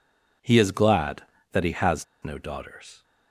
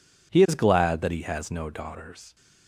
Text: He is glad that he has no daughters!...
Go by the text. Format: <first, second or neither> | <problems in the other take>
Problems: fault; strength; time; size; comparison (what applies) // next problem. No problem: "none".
second | pauses between "has" and "no"; slight; at 2.0 s; 0.19 s long